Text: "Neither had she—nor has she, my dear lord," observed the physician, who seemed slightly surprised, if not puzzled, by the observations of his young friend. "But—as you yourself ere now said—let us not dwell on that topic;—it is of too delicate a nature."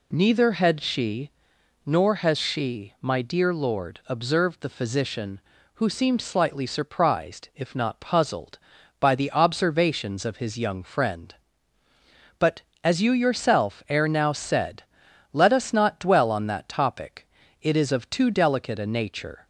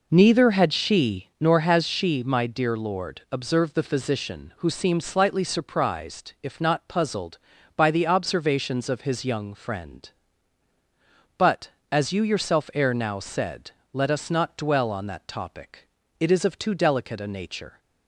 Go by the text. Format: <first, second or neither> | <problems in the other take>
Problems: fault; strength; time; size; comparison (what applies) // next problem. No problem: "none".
first | starts louder than the rest; noticeable; until 1.5 s; 4.5 dB